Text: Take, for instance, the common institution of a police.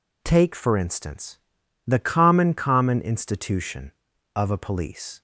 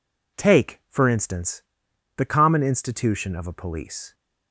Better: second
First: says "common" twice; at 2.5 s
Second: none

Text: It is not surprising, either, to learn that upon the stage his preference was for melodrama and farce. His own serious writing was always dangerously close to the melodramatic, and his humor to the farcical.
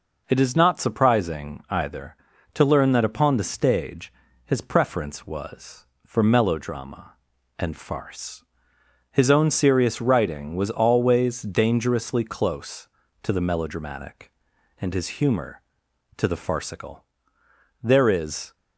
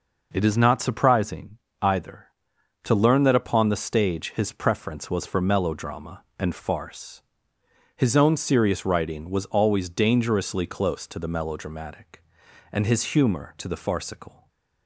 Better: second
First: pauses between "stage" and "his"; slight; at 4.1 s; 0.36 s long // goes on to say "There is"; noticeable; from 17.8 s on; 0.72 s long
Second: none

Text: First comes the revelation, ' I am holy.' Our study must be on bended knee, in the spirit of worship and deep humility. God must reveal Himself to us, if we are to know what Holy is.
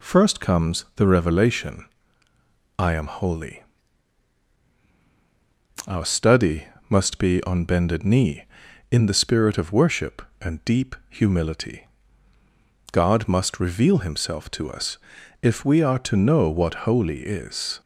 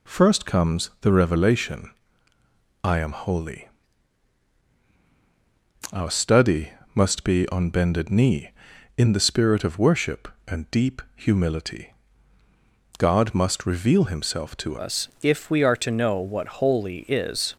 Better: first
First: pauses between "study" and "must"; slight; at 6.6 s; 0.24 s long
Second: pauses between "study" and "must"; slight; at 6.7 s; 0.24 s long // changes voice at "us"; from 14.7 s on; 2.8 s long

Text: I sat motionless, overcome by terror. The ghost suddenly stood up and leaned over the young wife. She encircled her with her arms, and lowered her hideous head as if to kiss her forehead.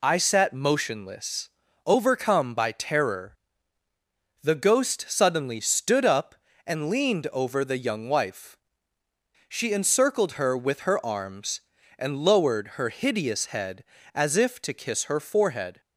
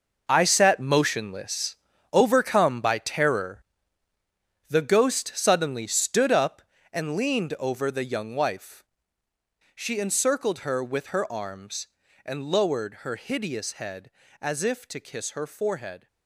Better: first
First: none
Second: gets quieter; strong; throughout; 11.5 dB

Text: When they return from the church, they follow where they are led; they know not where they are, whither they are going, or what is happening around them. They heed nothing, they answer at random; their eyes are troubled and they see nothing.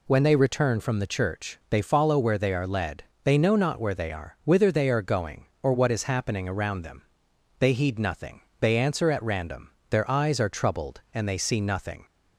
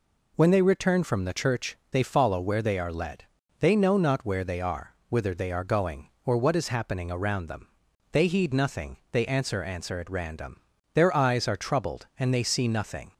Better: first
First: none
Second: says "answer" twice; at 9.6 s

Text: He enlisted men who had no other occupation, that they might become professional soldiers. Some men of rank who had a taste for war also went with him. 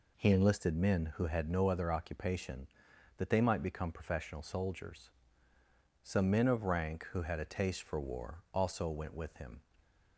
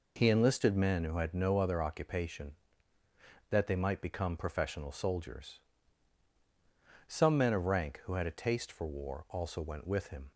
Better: neither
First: none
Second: none

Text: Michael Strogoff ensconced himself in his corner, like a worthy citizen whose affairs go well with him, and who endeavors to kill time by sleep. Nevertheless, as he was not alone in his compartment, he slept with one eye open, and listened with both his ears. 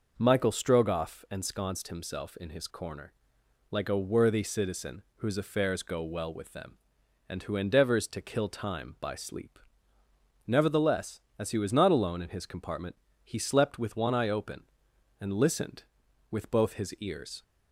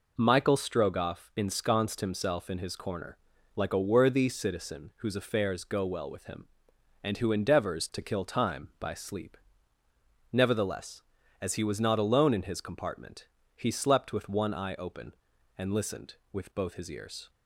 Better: second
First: says "them" for "him"; at 6.5 s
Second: none

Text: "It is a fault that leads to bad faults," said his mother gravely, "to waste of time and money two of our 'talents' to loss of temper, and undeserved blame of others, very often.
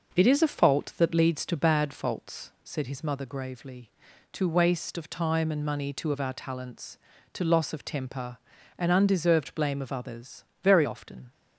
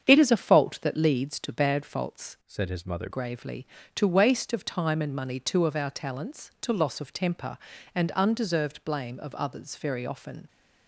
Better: first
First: none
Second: starts louder than the rest; strong; until 1.0 s; 7.5 dB // changes voice from "said" to "mother"; from 2.4 to 3.0 s; 0.6 s long

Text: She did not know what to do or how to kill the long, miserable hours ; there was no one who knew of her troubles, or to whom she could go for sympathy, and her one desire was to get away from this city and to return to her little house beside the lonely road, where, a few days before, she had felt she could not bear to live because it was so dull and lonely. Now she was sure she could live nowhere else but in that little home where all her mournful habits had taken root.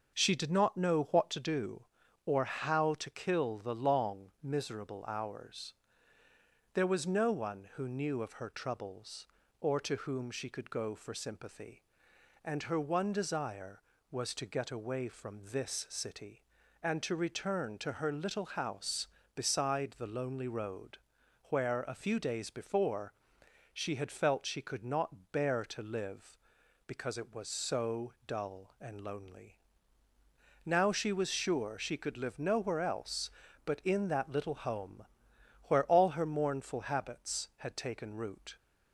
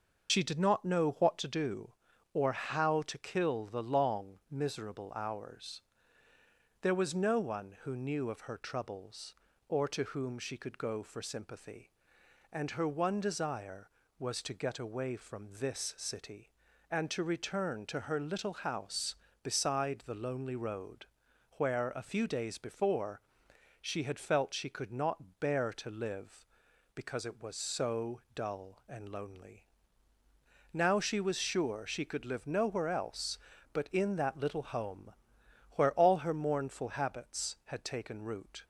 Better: first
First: pauses between "home" and "where"; noticeable; at 35.0 s; 0.60 s long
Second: loses the start of "She"; at 0.2 s; 80 ms // starts louder than the rest; until 1.3 s; 6.5 dB // pauses between "home" and "where"; noticeable; at 35.1 s; 0.60 s long

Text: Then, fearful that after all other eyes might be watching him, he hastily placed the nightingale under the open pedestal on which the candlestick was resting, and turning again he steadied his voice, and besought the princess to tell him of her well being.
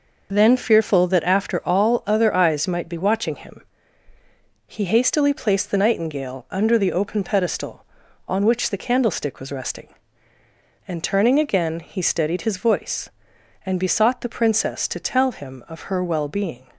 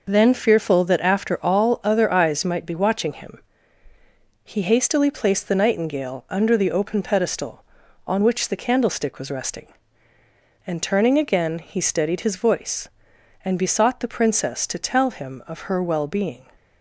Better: neither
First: none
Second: none

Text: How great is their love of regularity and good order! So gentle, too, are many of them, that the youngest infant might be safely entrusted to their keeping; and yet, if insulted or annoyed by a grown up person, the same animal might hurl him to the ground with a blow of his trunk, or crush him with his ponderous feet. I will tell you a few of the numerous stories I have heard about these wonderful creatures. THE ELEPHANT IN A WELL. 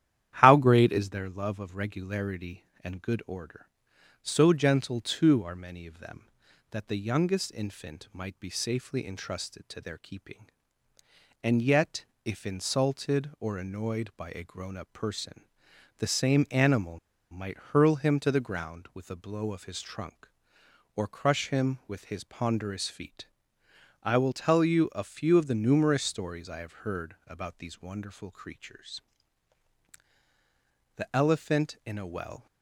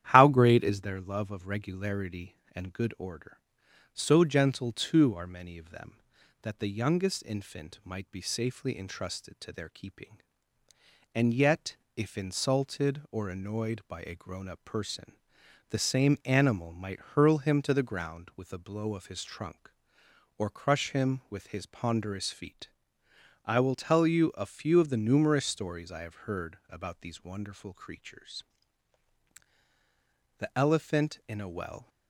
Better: second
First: starts louder than the rest; strong; until 1.3 s; 11 dB // pauses between "animal" and "might"; slight; at 16.9 s; 0.32 s long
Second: starts louder than the rest; strong; until 1.1 s; 11 dB

